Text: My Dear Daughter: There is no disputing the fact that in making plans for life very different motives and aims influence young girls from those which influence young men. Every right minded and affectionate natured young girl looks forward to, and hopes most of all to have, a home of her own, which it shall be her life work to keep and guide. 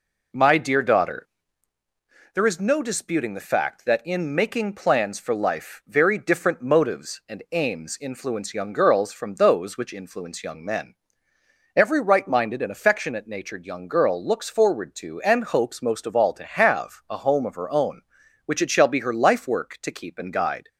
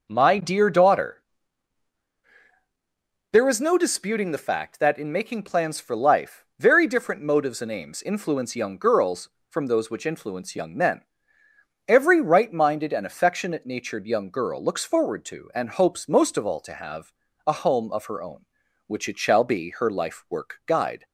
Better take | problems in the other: first | skips "to keep and"; at 20.6 s

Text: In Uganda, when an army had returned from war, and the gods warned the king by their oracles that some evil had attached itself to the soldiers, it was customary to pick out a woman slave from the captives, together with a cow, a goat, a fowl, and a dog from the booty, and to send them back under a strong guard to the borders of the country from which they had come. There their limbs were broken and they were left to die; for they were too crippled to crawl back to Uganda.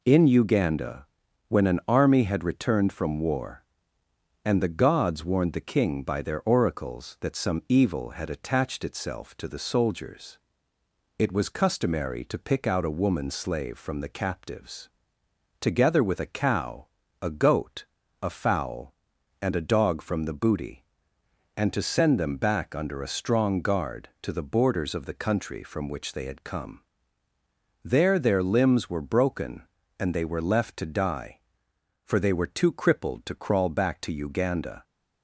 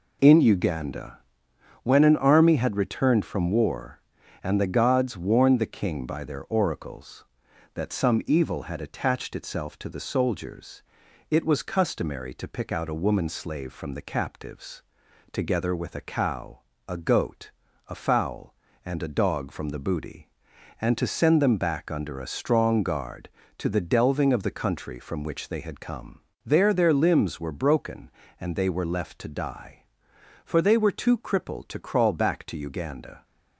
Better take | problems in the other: first | says "delving" for "borders"; at 23.8 s

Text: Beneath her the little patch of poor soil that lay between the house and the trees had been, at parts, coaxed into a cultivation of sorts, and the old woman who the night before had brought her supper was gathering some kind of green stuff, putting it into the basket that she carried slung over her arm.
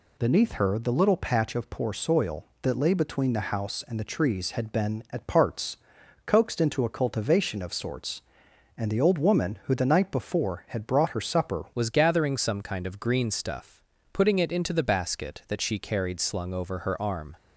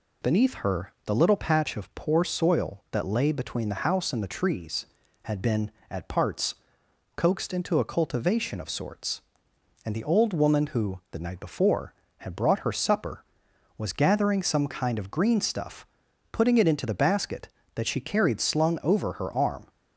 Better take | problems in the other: second | changes voice at "was"; from 11.7 s on; 5.6 s long

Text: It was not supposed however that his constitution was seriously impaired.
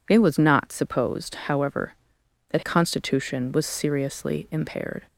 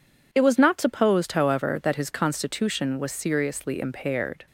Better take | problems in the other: second | skips "his"; at 2.6 s

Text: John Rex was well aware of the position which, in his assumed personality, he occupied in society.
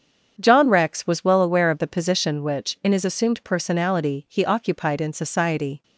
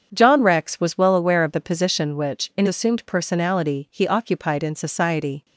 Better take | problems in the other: first | starts louder than the rest; strong; until 1.1 s; 7.5 dB; strong in the first // skips "his"; at 2.6 s

